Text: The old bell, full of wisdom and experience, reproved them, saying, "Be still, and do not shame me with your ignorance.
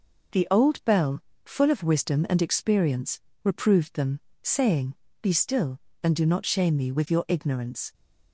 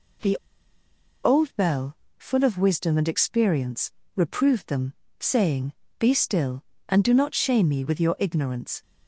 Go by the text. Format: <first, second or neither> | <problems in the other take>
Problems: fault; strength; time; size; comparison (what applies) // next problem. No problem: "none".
first | pauses between "The" and "old"; noticeable; at 0.3 s; 0.87 s long